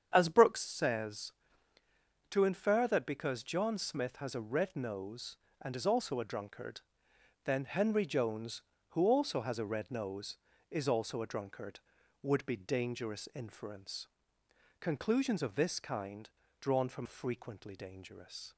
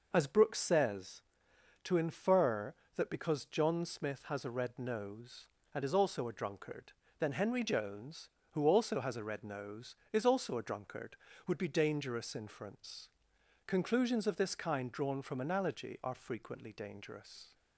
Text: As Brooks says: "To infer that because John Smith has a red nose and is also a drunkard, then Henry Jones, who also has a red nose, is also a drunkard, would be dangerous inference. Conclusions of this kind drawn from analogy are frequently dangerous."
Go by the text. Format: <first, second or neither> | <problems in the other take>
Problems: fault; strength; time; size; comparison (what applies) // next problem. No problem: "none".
second | starts louder than the rest; strong; until 1.1 s; 8 dB // pauses between "kind" and "drawn"; slight; at 16.2 s; 0.32 s long // skips "analogy are"; at 17.0 s